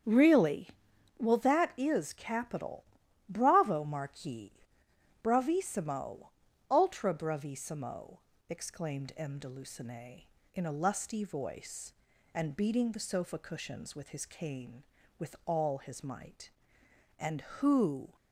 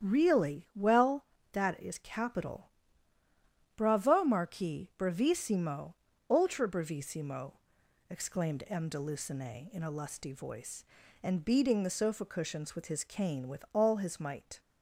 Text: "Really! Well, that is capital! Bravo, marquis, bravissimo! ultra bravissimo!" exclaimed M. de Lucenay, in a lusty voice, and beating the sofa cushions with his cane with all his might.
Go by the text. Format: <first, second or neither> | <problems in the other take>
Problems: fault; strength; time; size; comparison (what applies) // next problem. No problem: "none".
second | starts louder than the rest; strong; until 1.5 s; 8 dB; strong in the second // goes on to say "And who"; noticeable; from 17.1 s on; 0.96 s long